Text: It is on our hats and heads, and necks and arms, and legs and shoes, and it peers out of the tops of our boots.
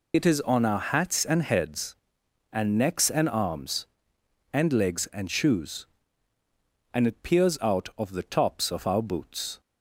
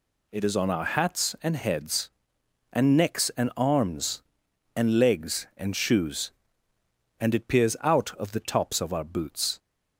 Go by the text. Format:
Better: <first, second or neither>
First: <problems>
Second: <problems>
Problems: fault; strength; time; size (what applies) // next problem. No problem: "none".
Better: second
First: loses the start of "It"; at 0.1 s; 45 ms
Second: none